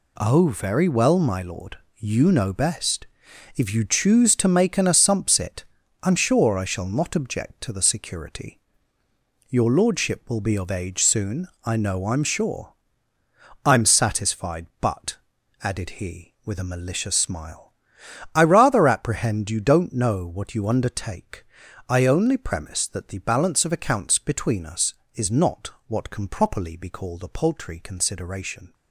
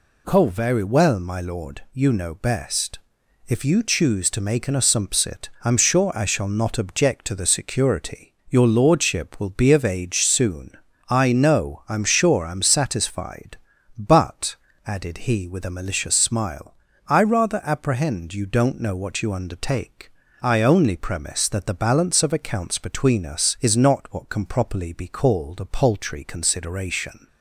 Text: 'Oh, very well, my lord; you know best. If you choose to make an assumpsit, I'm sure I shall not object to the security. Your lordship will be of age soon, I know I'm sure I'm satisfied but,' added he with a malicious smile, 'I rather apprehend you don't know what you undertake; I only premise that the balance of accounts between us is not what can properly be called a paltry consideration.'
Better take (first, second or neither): second